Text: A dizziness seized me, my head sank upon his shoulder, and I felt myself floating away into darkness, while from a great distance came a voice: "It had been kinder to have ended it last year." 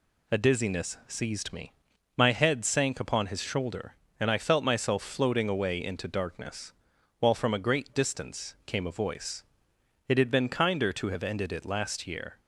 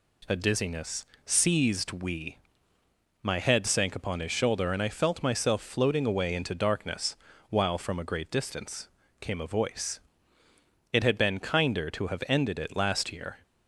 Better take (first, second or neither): first